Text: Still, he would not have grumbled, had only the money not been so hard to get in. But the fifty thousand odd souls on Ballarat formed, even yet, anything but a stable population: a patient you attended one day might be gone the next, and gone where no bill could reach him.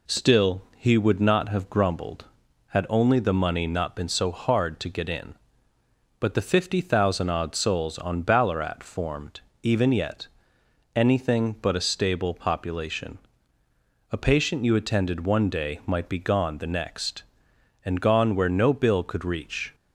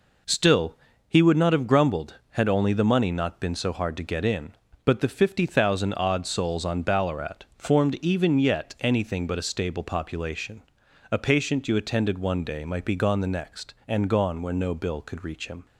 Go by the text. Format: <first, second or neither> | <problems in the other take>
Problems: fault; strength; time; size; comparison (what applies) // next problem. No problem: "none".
second | stops before "him"; at 19.7 s